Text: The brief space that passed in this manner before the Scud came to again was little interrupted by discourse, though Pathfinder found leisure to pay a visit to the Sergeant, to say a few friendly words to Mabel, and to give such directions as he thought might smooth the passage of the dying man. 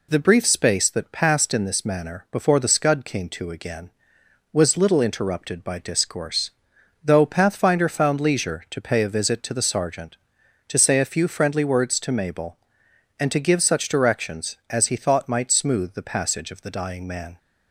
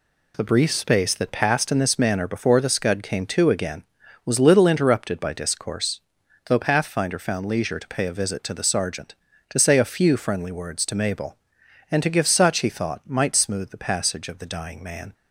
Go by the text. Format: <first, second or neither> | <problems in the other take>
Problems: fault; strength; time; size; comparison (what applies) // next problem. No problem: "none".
first | skips "directions as"; at 12.5 s